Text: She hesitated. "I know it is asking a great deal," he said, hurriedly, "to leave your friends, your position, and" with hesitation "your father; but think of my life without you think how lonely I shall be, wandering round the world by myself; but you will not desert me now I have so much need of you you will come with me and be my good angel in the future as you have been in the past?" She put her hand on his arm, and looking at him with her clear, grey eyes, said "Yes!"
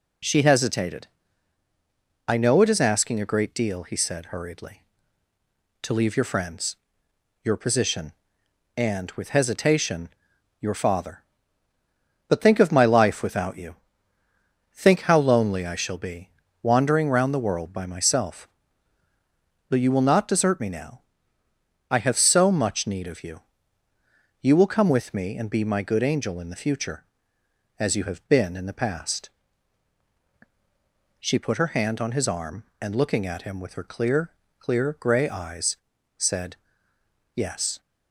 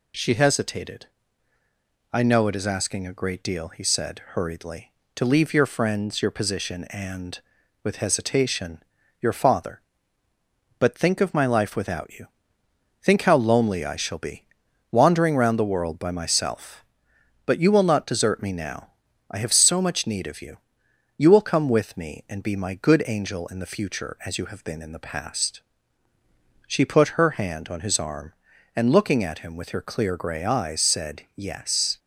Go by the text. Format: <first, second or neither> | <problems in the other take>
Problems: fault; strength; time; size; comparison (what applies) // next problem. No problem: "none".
second | pauses between "hesitation" and "your"; noticeable; at 10.0 s; 0.54 s long; also in the second // pauses between "you" and "think"; noticeable; at 13.7 s; 0.96 s long; noticeable in the second // pauses between "now" and "I"; noticeable; at 21.0 s; 0.88 s long; also in the second // pauses between "you" and "you"; noticeable; at 23.4 s; 0.98 s long; noticeable in the second // says "clear" twice; at 34.5 s // pauses between "said" and "Yes"; noticeable; at 36.5 s; 0.80 s long